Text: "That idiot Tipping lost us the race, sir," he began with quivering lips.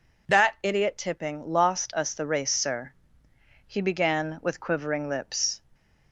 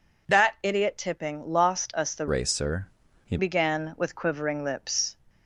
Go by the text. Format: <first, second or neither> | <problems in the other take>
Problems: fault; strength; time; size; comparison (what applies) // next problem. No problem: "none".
first | changes voice from "race" to "he"; from 2.2 to 3.3 s; 1.1 s long